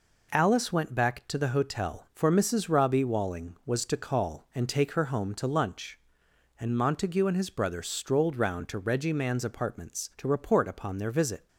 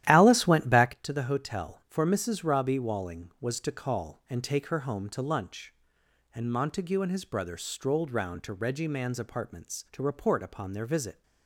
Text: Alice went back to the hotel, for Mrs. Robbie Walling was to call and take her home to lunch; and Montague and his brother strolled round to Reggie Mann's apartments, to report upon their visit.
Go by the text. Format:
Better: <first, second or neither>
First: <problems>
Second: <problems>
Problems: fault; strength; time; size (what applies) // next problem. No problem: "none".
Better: first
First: none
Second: starts louder than the rest; strong; until 0.9 s; 12.5 dB